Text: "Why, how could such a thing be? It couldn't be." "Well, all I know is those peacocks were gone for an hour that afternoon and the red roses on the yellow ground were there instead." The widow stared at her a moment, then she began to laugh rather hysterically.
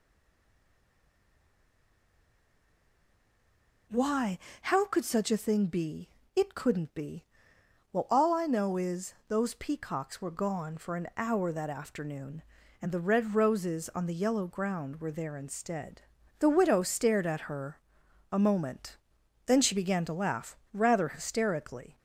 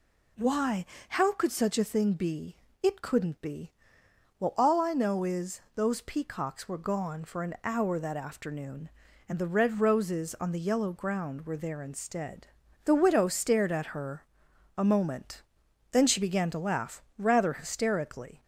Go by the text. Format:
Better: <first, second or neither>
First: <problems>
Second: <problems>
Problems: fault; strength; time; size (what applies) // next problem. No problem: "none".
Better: second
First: stays silent before the first word; strong; until 3.8 s; 3.8 s long // pauses between "her" and "a"; noticeable; at 17.7 s; 0.54 s long // pauses between "laugh" and "rather"; slight; at 20.5 s; 0.16 s long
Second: pauses between "her" and "a"; noticeable; at 14.2 s; 0.54 s long // pauses between "laugh" and "rather"; slight; at 17.0 s; 0.16 s long